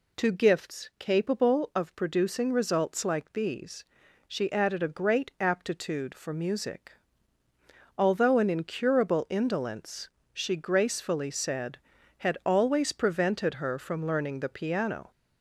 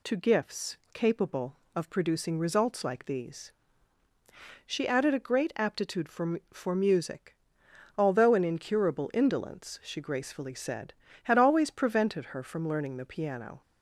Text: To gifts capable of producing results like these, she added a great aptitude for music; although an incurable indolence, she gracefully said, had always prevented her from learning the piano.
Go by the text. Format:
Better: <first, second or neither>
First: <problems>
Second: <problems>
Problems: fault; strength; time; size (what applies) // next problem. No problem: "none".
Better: first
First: none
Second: pauses between "gifts" and "capable"; slight; at 0.7 s; 0.18 s long // says "for" twice; at 6.5 s